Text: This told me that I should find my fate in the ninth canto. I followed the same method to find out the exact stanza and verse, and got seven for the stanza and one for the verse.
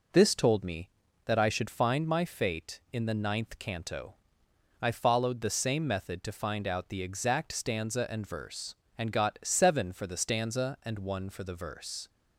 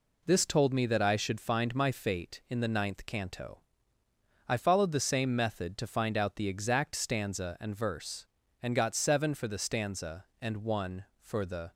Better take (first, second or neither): first